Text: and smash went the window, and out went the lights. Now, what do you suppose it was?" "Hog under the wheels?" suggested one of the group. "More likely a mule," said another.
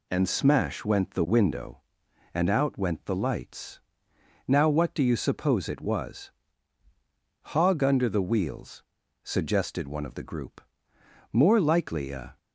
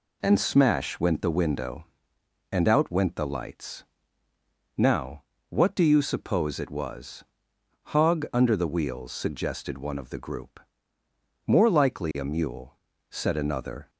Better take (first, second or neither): second